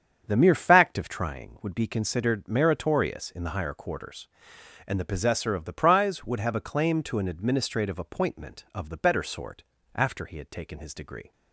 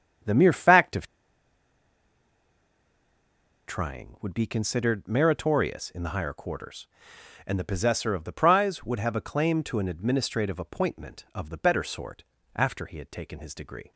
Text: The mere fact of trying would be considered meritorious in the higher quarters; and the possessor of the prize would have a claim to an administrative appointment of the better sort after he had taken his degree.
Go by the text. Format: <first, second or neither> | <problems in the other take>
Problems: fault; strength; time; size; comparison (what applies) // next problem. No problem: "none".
first | starts louder than the rest; strong; until 3.8 s; 8 dB; strong in the first // pauses between "of" and "trying"; strong; at 1.0 s; 2.6 s long // pauses between "sort" and "after"; slight; at 12.2 s; 0.32 s long; slight in the first